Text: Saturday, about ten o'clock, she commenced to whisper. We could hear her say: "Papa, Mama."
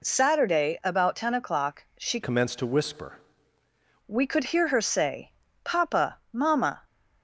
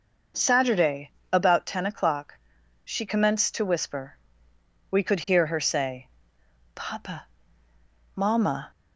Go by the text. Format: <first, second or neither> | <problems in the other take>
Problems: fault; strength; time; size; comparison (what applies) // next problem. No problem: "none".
second | changes voice from "commenced" to "whisper"; from 2.2 to 3.1 s; 0.9 s long